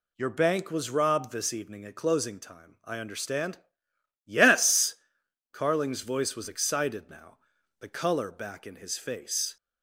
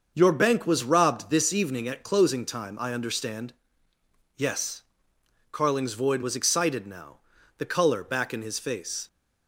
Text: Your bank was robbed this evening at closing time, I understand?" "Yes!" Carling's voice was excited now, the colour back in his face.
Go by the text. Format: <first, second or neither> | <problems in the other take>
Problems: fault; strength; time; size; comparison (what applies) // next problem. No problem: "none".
first | starts louder than the rest; until 1.1 s; 6.5 dB // says "void" for "voice"; at 5.9 s